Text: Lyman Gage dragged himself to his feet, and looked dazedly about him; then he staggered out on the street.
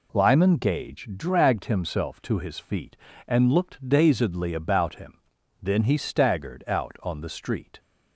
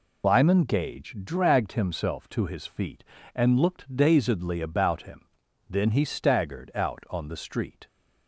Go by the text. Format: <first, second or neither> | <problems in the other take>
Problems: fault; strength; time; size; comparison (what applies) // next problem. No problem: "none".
first | loses the start of "Lyman"; at 0.2 s; 75 ms